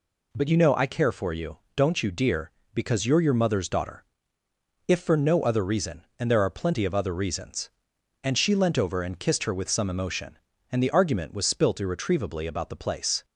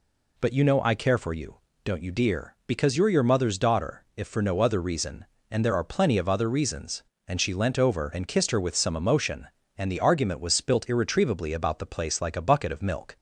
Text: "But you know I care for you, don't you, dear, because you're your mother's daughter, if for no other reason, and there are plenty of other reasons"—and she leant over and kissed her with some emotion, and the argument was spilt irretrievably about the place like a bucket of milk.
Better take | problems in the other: second | stops before "like a bucket of milk"; at 13.2 s

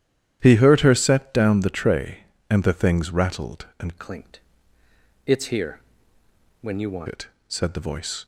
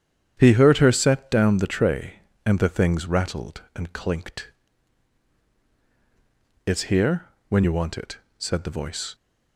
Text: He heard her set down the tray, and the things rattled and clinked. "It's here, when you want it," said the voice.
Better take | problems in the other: second | starts louder than the rest; strong; until 1.4 s; 11 dB; strong in the second // changes voice from "clinked" to "want"; from 3.9 to 7.0 s; 3.1 s long

